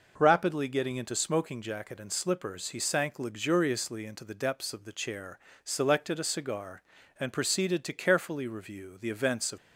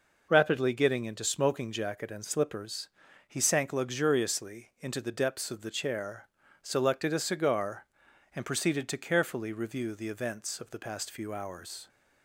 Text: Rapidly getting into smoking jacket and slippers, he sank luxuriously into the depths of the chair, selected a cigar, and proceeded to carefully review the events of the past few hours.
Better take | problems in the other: second | stops before "the past few hours"; at 9.5 s

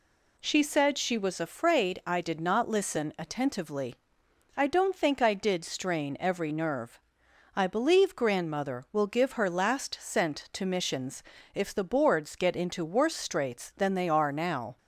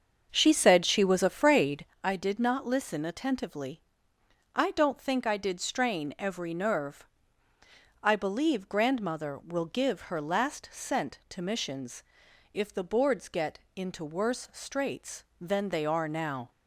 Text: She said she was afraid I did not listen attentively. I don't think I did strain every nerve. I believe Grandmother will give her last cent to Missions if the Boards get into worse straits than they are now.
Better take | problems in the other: first | starts louder than the rest; until 1.9 s; 7 dB // pauses between "afraid" and "I"; slight; at 1.8 s; 0.20 s long // pauses between "Missions" and "if"; noticeable; at 12.0 s; 0.50 s long; slight in the first // pauses between "get" and "into"; slight; at 13.5 s; 0.16 s long

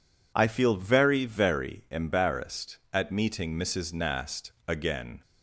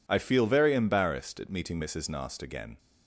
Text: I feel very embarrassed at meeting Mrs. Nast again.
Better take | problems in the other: second | says "very" twice; at 1.2 s

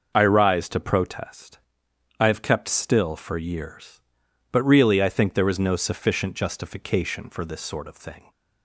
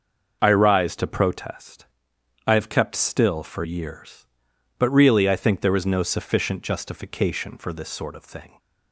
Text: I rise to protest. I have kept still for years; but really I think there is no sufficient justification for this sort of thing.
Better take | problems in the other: neither | none

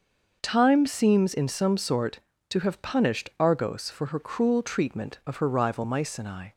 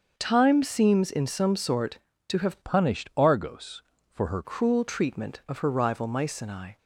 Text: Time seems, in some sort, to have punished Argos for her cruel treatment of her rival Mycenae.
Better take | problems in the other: first | starts louder than the rest; until 1.1 s; 6.5 dB; also in the first // changes voice from "punished" to "her"; from 2.6 to 4.4 s; 1.8 s long

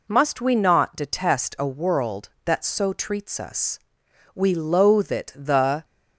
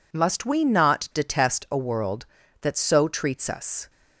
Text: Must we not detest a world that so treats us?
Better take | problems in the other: second | goes on to say "We loathe it the"; from 4.3 s on; 1.5 s long

